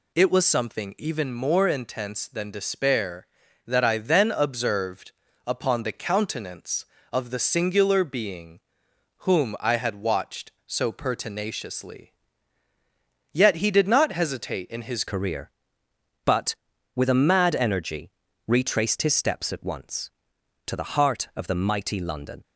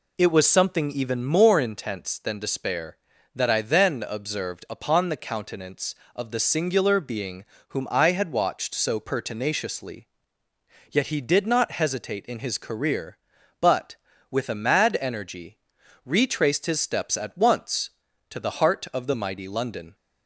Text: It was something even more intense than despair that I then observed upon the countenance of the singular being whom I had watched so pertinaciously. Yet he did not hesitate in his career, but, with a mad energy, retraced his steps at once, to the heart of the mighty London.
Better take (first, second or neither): second